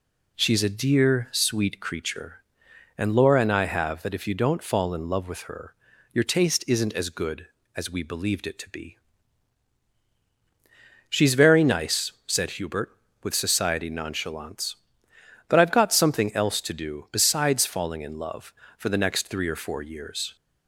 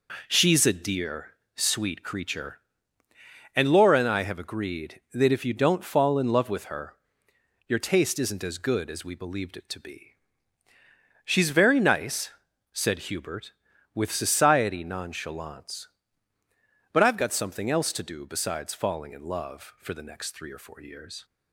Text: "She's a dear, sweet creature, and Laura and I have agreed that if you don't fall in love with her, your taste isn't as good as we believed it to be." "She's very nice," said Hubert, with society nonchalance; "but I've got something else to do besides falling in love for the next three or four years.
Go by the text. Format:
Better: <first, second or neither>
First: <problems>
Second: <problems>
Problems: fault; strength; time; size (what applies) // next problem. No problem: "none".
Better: second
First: skips "agreed"; at 4.0 s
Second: none